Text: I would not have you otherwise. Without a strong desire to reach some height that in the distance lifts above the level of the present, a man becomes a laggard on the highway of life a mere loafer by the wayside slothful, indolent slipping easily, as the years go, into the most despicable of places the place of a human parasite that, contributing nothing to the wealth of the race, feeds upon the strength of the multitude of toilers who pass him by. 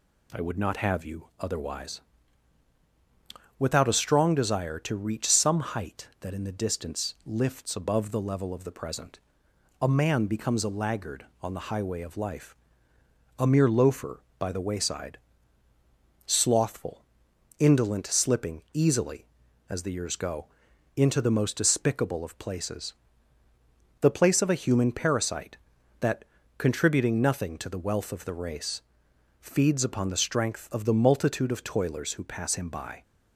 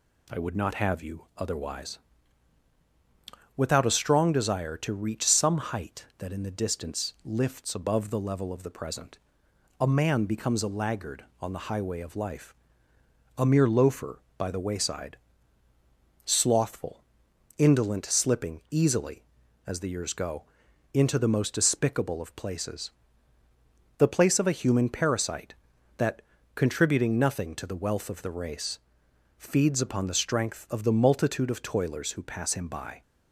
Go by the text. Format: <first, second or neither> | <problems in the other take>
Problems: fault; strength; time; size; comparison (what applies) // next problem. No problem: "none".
neither | pauses between "life" and "a"; noticeable; the same in both // pauses between "wayside" and "slothful"; the same in both // pauses between "places" and "the"; the same in both